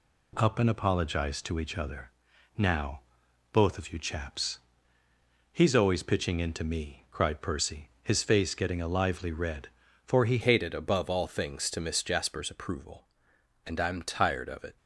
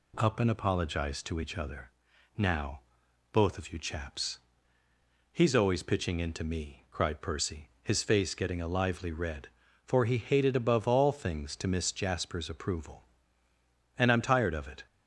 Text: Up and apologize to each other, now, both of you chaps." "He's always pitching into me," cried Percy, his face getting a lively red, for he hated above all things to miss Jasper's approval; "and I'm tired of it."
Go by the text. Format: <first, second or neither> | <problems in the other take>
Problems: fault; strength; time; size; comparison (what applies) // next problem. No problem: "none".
second | changes voice at "hated"; from 10.4 s on; 4.3 s long